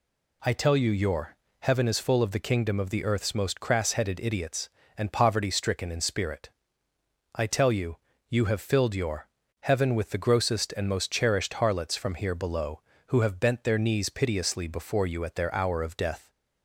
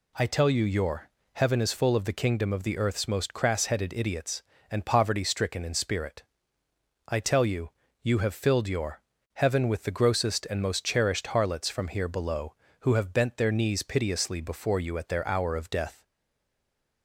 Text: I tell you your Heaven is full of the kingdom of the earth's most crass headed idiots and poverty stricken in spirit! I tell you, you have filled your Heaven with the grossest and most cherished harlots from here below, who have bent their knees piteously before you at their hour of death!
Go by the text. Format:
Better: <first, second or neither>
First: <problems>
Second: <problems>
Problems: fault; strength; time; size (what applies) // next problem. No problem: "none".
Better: first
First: pauses between "your" and "Heaven"; slight; at 1.3 s; 0.26 s long // pauses between "your" and "Heaven"; slight; at 9.2 s; 0.36 s long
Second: pauses between "your" and "Heaven"; slight; at 1.0 s; 0.26 s long // pauses between "your" and "Heaven"; slight; at 8.9 s; 0.36 s long // stays silent after the last word; from 16.0 s on; 1.0 s long